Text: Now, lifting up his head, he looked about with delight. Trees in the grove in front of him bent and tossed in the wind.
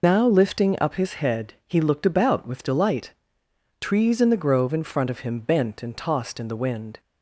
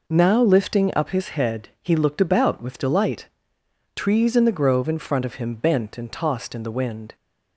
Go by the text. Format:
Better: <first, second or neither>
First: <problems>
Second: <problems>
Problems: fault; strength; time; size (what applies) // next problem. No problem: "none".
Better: second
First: loses the start of "Now"; at 0.0 s; 95 ms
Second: none